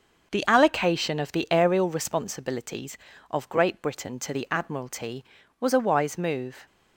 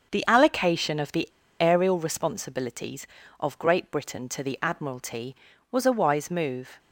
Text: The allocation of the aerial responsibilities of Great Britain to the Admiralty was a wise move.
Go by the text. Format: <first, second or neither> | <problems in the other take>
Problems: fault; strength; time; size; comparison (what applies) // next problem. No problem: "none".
first | starts louder than the rest; until 1.1 s; 6.5 dB; also in the first // pauses between "the" and "aerial"; slight; at 1.2 s; 0.33 s long